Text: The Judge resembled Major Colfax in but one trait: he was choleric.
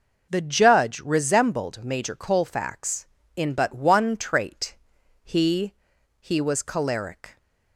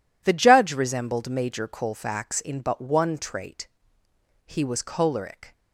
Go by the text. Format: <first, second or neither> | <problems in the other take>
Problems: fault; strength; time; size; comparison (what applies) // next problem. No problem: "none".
second | says "he" twice; at 6.1 s